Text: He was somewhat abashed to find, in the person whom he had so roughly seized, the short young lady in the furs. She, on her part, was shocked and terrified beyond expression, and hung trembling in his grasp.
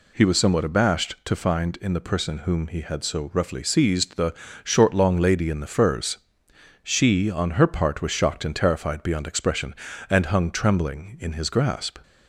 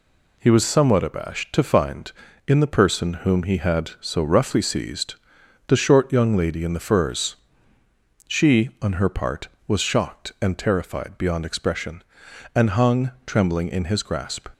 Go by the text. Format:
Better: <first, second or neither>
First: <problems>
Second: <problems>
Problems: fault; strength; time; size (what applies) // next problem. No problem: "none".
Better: second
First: pauses between "the" and "short"; slight; at 4.3 s; 0.30 s long // says "long" for "young"; at 4.9 s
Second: none